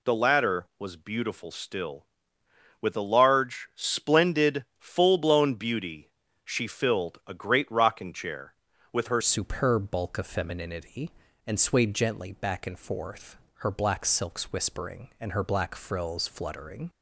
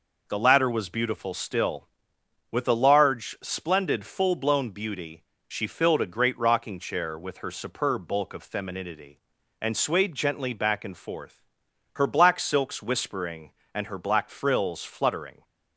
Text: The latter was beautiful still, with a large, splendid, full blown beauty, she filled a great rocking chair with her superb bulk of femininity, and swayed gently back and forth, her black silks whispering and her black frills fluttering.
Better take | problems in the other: second | changes voice at "superb"; from 9.2 s on; 7.6 s long

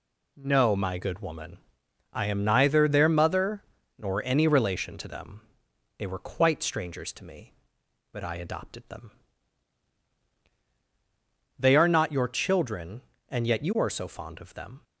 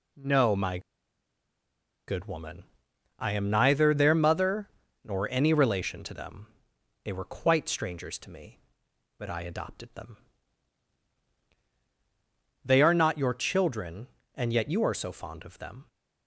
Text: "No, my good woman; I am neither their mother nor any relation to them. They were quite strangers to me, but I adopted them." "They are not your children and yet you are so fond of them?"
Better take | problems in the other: first | pauses between "my" and "good"; strong; at 0.7 s; 1.2 s long // pauses between "mother" and "nor"; slight; at 4.6 s; 0.34 s long; slight in the first

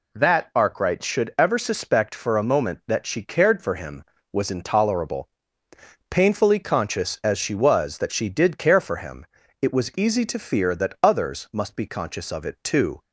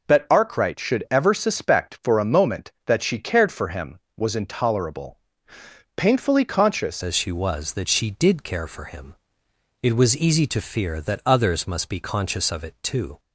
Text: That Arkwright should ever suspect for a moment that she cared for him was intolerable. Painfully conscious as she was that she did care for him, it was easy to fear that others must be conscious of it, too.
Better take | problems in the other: first | changes voice at "as"; from 7.0 s on; 6.1 s long

